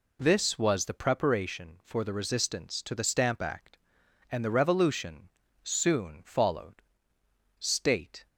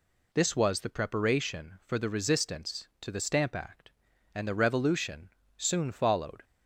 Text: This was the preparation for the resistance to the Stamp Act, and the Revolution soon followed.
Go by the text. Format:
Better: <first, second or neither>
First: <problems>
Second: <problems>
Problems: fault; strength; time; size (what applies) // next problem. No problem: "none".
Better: second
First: pauses between "Revolution" and "soon"; slight; at 5.3 s; 0.32 s long // goes on to say "State"; noticeable; from 7.5 s on; 0.68 s long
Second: pauses between "Revolution" and "soon"; slight; at 5.2 s; 0.28 s long